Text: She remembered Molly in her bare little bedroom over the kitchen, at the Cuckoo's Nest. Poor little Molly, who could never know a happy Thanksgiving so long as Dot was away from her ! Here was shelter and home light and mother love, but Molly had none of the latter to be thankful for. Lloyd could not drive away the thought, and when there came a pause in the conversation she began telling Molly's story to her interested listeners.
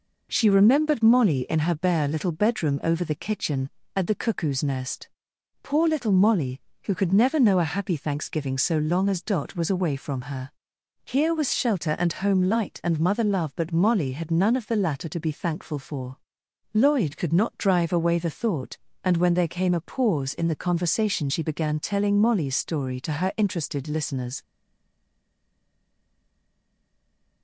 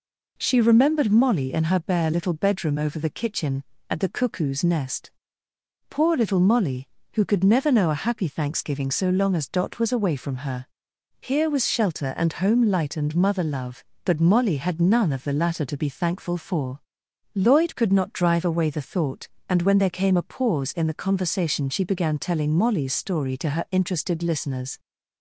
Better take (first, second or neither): second